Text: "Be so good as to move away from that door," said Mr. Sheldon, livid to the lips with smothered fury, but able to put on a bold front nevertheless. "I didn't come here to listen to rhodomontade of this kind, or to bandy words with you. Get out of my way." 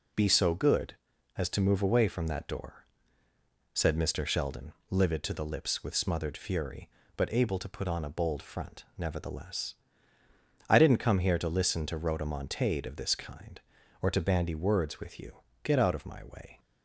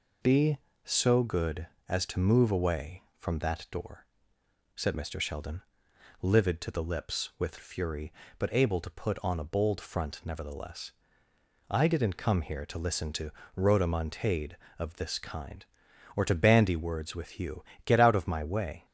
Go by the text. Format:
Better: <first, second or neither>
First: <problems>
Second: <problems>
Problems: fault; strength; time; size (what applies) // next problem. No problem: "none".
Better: first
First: none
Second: skips "smothered"; at 7.5 s // pauses between "to" and "rhodomontade"; slight; at 13.3 s; 0.24 s long